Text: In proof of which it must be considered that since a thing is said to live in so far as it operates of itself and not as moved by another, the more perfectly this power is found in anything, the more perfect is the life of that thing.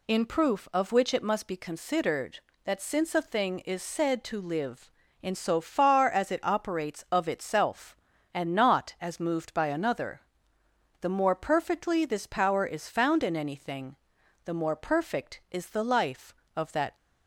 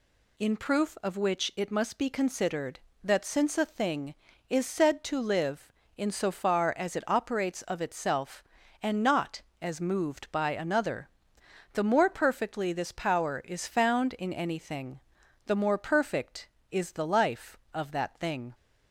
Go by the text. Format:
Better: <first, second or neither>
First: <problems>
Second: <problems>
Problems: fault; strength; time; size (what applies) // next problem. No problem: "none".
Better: second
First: stops before "thing"; at 16.9 s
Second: none